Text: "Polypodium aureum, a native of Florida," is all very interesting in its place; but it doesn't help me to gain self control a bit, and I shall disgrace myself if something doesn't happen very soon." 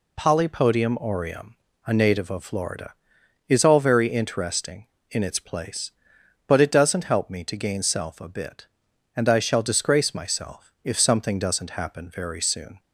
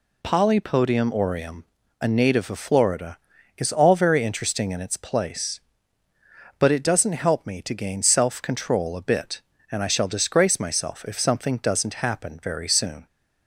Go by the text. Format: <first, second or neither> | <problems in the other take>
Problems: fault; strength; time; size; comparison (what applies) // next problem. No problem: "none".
second | skips "control"; at 8.2 s